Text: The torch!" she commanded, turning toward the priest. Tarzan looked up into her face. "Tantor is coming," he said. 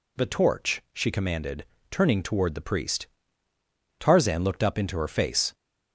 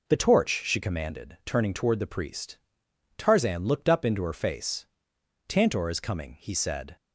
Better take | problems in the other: second | stops before "Tantor is coming he said"; at 5.5 s

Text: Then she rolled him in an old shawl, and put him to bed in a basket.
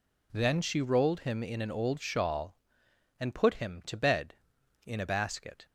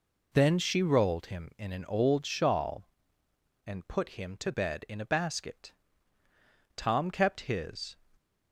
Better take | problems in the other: first | goes on to say "Tom kept his"; noticeable; from 6.7 s on; 1.2 s long

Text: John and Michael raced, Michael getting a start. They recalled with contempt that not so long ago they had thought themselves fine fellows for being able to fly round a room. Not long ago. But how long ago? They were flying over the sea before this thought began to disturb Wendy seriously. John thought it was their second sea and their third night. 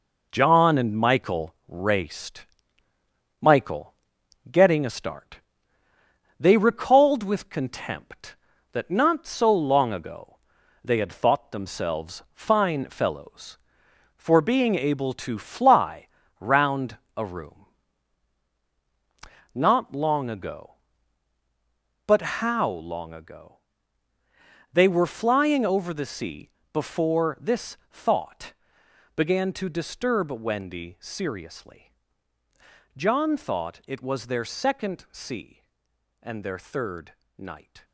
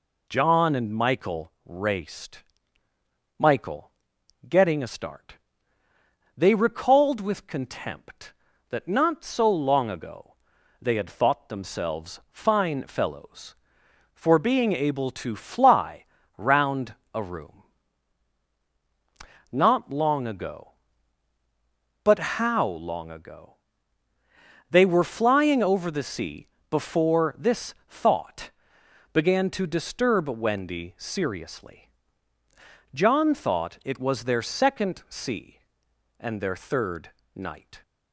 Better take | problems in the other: second | gets quieter; noticeable; throughout; 6 dB // pauses between "Michael" and "getting"; noticeable; at 3.9 s; 0.54 s long; noticeable in the second // pauses between "ago" and "they"; noticeable; at 10.3 s; 0.48 s long; noticeable in the second // pauses between "fly" and "round"; slight; at 16.0 s; 0.32 s long; slight in the second // pauses between "round" and "a"; slight; at 16.9 s; 0.20 s long; slight in the second // pauses between "sea" and "before"; slight; at 26.4 s; 0.24 s long; slight in the second // pauses between "thought" and "began"; noticeable; at 28.5 s; 0.62 s long; noticeable in the second // pauses between "third" and "night"; slight; at 37.1 s; 0.24 s long; slight in the second

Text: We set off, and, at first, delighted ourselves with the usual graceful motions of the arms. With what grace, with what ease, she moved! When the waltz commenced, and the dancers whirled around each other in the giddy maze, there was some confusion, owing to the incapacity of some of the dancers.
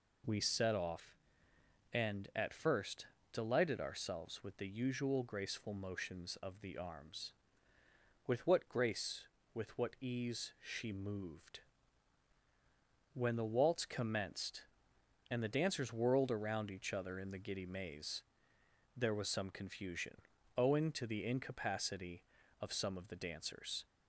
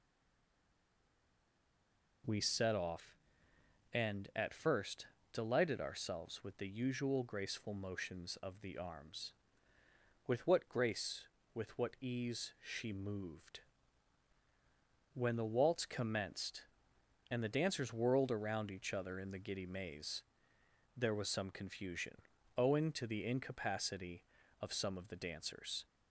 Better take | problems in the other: first | stays silent before the first word; until 2.2 s; 2.2 s long

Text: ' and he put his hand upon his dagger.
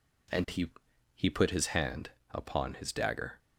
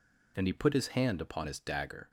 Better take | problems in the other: second | says "he" twice; at 1.1 s // pauses between "hand" and "upon"; slight; at 2.1 s; 0.22 s long

